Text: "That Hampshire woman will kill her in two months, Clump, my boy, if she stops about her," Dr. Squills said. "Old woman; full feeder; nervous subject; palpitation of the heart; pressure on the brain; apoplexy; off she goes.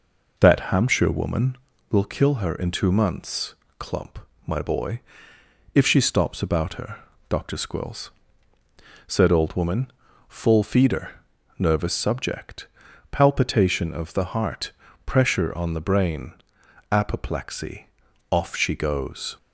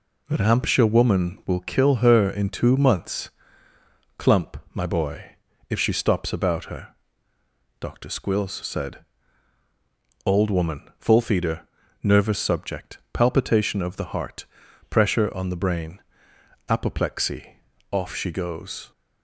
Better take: second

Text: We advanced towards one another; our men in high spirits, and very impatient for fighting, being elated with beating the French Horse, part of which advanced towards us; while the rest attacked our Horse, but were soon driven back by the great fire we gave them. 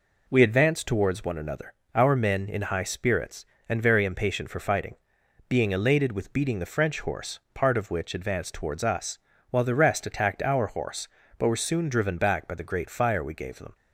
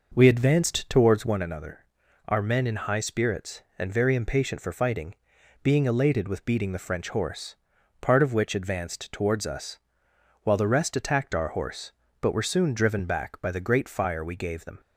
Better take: first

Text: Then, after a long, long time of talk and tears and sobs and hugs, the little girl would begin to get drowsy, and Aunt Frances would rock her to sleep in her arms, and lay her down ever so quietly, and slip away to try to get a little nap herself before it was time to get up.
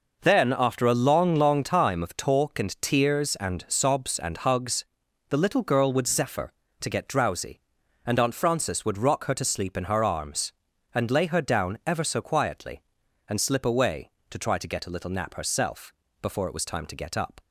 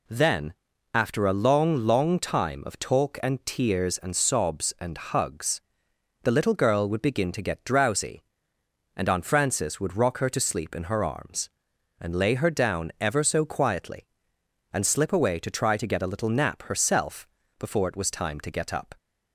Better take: second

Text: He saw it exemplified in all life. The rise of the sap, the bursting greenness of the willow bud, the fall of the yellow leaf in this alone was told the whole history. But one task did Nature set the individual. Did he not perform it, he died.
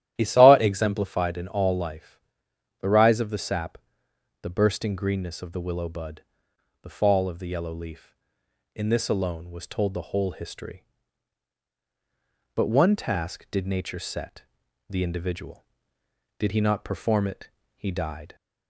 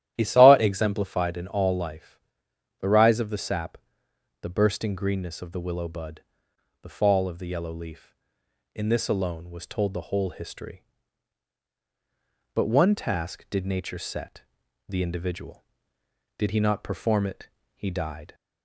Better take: neither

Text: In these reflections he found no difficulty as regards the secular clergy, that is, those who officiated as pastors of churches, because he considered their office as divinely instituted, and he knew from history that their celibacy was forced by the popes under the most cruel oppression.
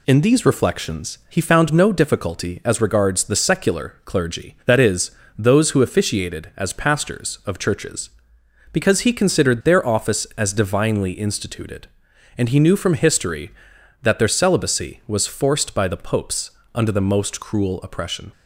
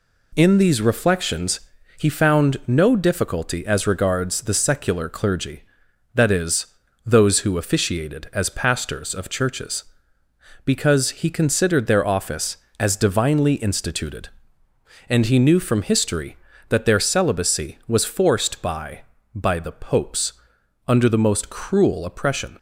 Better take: first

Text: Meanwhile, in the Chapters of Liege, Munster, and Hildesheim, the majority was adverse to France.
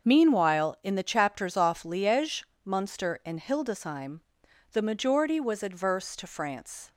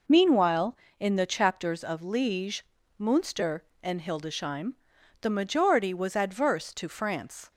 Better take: second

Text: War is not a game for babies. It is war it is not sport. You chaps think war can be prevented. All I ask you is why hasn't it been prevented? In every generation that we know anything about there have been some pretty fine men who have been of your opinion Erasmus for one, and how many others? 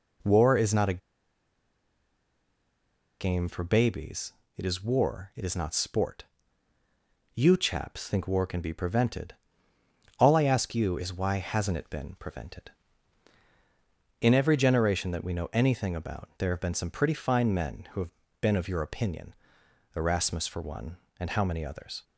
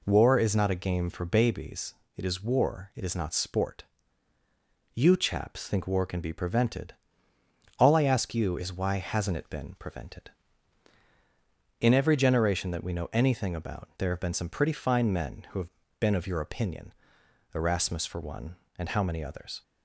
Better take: second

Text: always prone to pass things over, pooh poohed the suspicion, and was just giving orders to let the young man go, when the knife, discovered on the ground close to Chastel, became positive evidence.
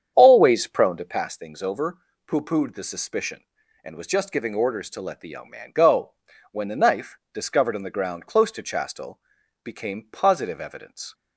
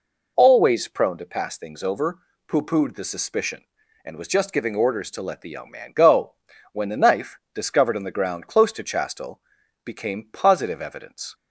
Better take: second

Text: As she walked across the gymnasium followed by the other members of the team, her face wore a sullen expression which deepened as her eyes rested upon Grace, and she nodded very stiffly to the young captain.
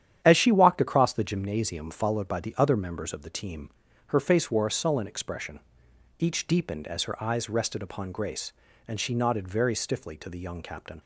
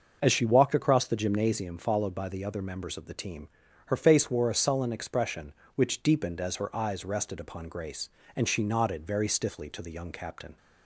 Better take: second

